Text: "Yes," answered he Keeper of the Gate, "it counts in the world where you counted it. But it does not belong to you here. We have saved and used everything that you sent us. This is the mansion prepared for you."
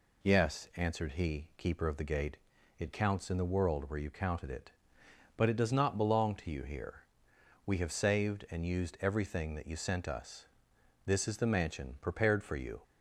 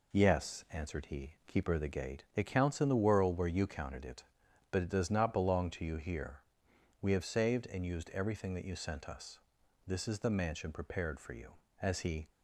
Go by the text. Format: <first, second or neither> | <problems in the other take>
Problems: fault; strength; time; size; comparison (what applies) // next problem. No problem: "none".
first | goes on to say "As he"; slight; from 11.8 s on; 0.46 s long